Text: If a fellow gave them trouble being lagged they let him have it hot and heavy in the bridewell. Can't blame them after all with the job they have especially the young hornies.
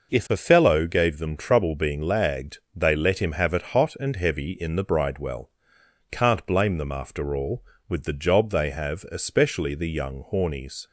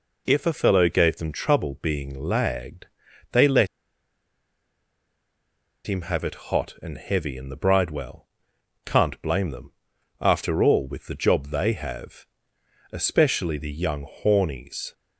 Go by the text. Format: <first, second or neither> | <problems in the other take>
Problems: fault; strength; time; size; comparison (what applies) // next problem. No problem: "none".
first | pauses between "lagged" and "they"; at 2.8 s; 0.44 s long; slight in the first // pauses between "let" and "him"; strong; at 3.6 s; 2.1 s long // pauses between "them" and "after"; noticeable; at 9.7 s; 0.50 s long // pauses between "have" and "especially"; noticeable; at 12.2 s; 0.66 s long // pauses between "young" and "hornies"; slight; at 14.0 s; 0.18 s long